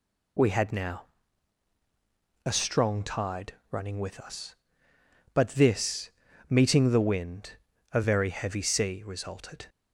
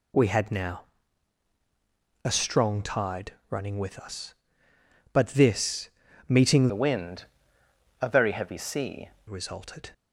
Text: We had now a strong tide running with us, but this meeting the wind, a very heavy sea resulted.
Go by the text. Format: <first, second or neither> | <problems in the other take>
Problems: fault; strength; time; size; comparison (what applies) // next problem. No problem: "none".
first | pauses between "now" and "a"; strong; at 0.8 s; 1.4 s long; strong in the first // pauses between "tide" and "running"; slight; at 3.3 s; 0.16 s long; slight in the first // pauses between "this" and "meeting"; at 5.8 s; 0.40 s long; also in the first // changes voice from "the" to "sea"; from 6.6 to 9.0 s; 2.4 s long